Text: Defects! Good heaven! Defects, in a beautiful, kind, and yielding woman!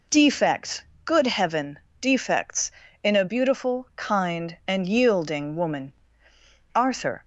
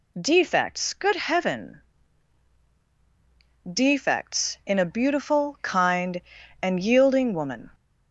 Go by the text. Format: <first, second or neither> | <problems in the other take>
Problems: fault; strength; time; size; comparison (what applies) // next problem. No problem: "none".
second | goes on to say "Arthur"; from 6.7 s on; 0.50 s long